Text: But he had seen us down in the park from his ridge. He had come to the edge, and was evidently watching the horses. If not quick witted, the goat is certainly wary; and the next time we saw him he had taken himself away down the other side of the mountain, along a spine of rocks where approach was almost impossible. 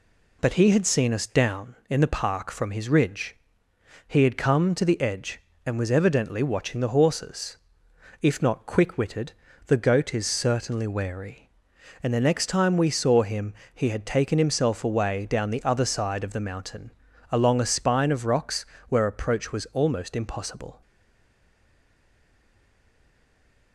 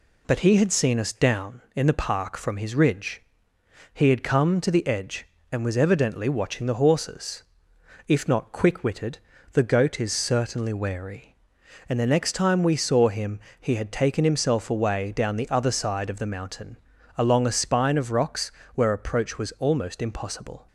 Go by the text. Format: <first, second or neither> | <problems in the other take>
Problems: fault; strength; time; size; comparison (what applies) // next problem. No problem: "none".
second | pauses between "him" and "he"; slight; at 13.5 s; 0.22 s long; slight in the second // pauses between "rocks" and "where"; slight; at 18.6 s; 0.22 s long; slight in the second // stays silent after the last word; strong; from 20.8 s on; 2.9 s long